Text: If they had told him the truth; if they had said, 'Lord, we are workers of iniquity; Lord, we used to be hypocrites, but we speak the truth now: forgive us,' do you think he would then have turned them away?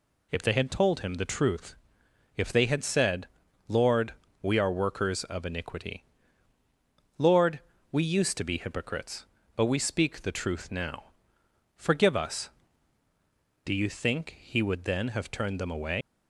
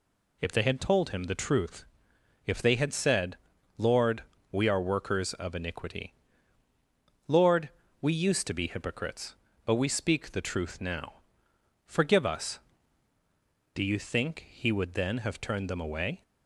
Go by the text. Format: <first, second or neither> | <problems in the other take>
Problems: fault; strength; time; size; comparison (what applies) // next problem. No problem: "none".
second | leaves "away" unfinished; at 16.0 s; 115 ms